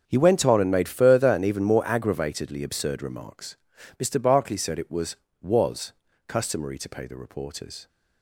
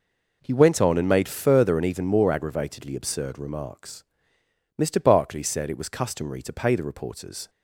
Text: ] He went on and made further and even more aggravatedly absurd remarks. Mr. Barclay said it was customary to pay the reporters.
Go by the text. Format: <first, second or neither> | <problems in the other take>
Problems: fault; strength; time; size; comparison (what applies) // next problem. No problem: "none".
second | starts louder than the rest; until 1.0 s; 7 dB // says "was" twice; at 5.4 s